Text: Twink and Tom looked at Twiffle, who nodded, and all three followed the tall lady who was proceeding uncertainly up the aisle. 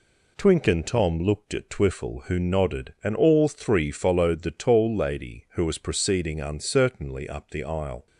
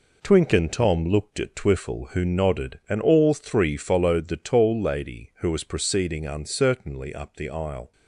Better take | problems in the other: first | gets quieter; throughout; 6.5 dB

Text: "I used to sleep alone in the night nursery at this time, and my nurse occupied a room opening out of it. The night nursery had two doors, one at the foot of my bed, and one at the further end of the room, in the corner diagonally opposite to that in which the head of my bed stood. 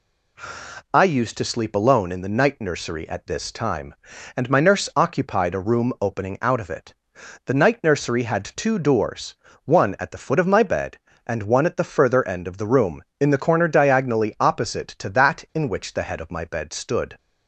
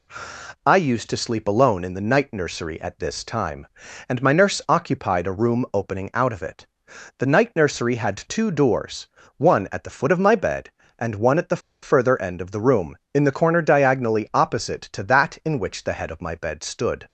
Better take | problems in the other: first | pauses between "the" and "further"; slight; at 11.5 s; 0.22 s long

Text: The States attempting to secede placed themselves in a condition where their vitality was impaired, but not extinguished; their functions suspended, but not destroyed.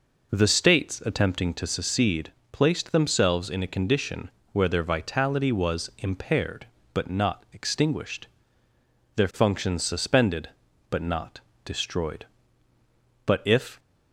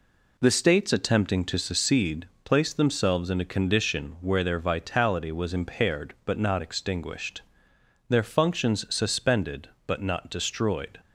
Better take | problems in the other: second | pauses between "secede" and "placed"; slight; at 2.3 s; 0.22 s long; slight in the second // pauses between "condition" and "where"; slight; at 4.3 s; 0.22 s long // pauses between "not" and "destroyed"; slight; at 11.4 s; 0.24 s long // goes on to say "But if"; from 13.2 s on; 0.52 s long

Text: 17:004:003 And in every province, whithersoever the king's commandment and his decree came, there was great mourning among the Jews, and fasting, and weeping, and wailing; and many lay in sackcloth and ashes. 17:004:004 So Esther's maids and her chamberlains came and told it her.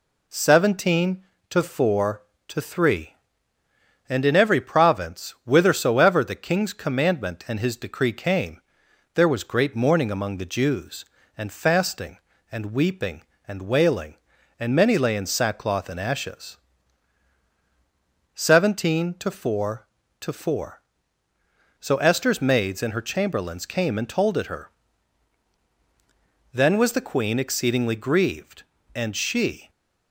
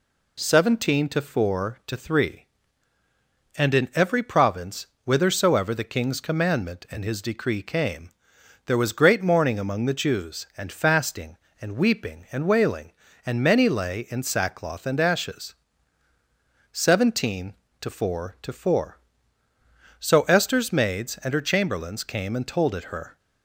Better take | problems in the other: second | goes on to say "Then was the queen exceedingly grieved and she"; strong; from 26.5 s on; 3.1 s long

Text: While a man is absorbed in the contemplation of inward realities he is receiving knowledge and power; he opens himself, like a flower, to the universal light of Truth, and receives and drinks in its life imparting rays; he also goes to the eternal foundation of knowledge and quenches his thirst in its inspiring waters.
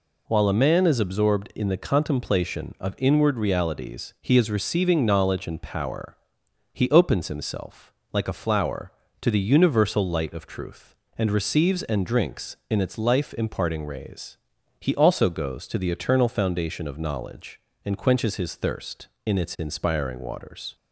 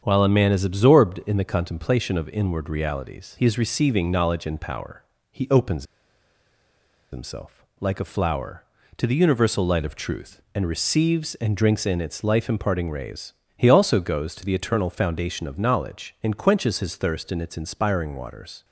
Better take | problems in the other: first | starts louder than the rest; strong; until 1.0 s; 7.5 dB // pauses between "opens" and "himself"; strong; at 5.8 s; 1.2 s long

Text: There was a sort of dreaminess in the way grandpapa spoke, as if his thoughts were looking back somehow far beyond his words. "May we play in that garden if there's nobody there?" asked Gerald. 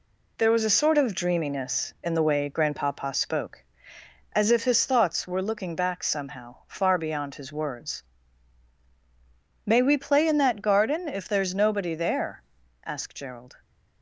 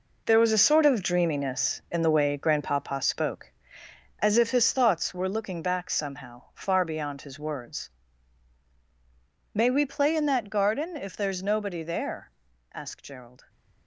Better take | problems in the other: first | gets quieter; strong; throughout; 9 dB

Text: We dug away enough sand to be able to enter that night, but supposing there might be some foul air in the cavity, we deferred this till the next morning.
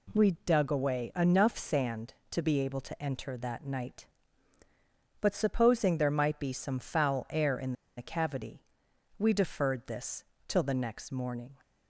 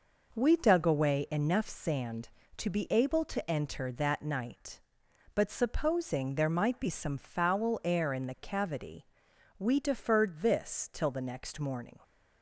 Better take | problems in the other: second | pauses between "in" and "the"; slight; at 7.7 s; 0.24 s long // pauses between "this" and "till"; slight; at 10.2 s; 0.24 s long

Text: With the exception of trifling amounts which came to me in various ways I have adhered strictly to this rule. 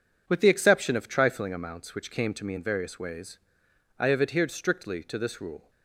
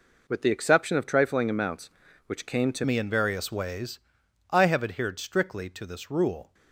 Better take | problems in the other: first | changes voice at "me"; from 2.8 s on; 3.7 s long // pauses between "ways" and "I"; noticeable; at 3.9 s; 0.54 s long; noticeable in the first

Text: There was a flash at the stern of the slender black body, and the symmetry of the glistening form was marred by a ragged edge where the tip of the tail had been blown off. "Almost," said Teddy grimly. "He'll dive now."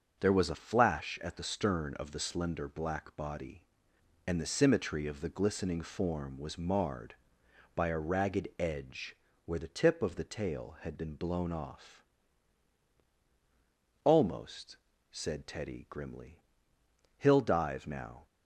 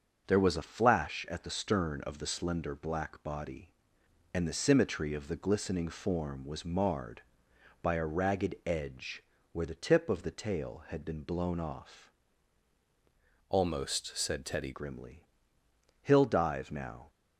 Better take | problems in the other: first | pauses between "edge" and "where"; slight; at 9.2 s; 0.28 s long; slight in the first // changes voice from "Almost" to "Teddy"; from 13.4 to 14.7 s; 1.3 s long

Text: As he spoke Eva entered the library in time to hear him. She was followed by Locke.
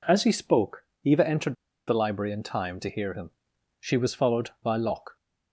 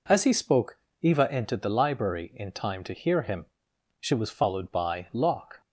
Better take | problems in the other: second | pauses between "spoke" and "Eva"; slight; at 0.8 s; 0.22 s long; slight in the second // pauses between "entered" and "the"; slight; at 1.5 s; 0.33 s long

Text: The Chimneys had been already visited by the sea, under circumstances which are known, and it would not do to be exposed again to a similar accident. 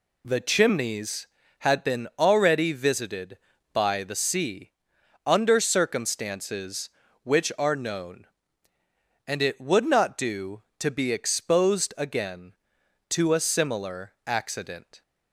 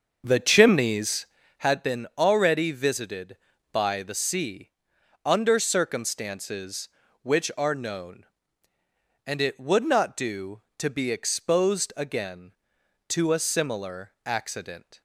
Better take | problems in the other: first | starts louder than the rest; until 1.7 s; 6.5 dB

